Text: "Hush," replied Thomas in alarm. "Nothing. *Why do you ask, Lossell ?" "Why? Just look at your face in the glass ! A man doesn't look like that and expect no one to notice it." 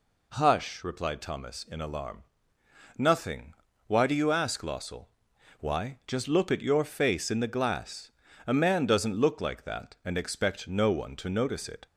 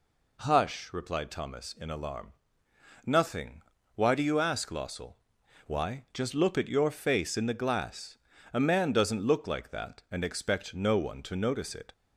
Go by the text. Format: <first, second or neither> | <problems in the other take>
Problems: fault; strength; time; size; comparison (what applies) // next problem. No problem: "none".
neither | none